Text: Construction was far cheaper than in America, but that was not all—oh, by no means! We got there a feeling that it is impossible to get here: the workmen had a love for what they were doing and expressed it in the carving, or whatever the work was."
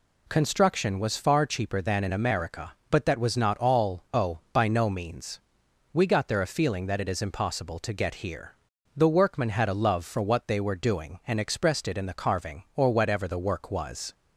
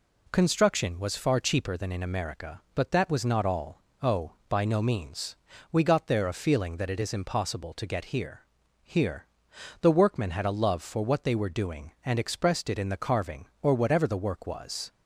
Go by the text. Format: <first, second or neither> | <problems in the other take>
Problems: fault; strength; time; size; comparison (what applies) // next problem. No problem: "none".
first | says "here" twice; at 8.8 s